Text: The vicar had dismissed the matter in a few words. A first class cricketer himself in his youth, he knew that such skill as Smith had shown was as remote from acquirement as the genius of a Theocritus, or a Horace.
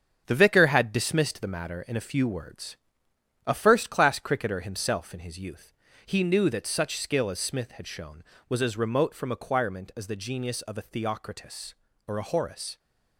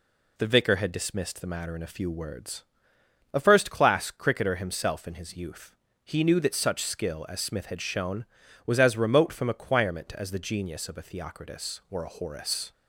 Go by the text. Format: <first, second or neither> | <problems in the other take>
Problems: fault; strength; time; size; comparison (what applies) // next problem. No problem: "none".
second | gets quieter; throughout; 6.5 dB